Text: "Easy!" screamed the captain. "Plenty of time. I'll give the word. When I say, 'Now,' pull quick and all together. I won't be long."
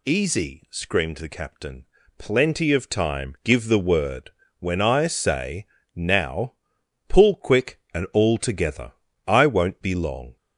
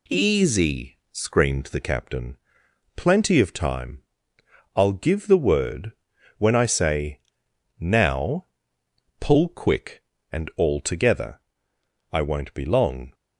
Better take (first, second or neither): second